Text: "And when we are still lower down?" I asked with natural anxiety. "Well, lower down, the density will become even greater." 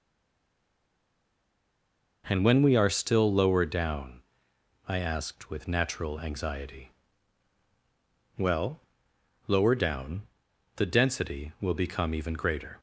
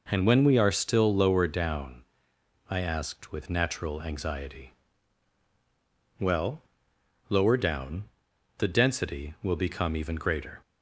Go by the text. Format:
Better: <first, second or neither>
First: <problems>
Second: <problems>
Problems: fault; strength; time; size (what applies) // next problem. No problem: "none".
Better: second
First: stays silent before the first word; until 2.2 s; 2.2 s long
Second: none